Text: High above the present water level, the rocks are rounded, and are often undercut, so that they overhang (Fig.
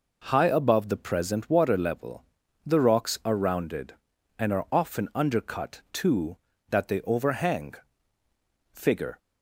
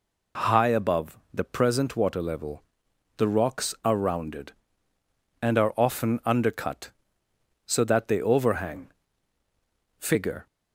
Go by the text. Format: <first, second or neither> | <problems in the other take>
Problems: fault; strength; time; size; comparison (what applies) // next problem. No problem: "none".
second | says "too" for "so"; at 5.9 s